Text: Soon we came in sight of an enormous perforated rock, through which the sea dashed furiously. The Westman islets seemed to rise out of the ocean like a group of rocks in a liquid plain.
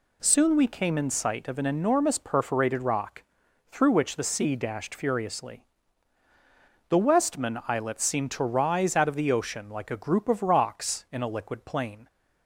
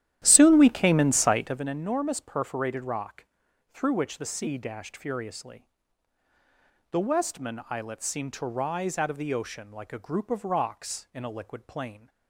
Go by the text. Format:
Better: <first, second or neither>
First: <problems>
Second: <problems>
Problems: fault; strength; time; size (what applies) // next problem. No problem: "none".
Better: first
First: none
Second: starts louder than the rest; strong; until 1.7 s; 12 dB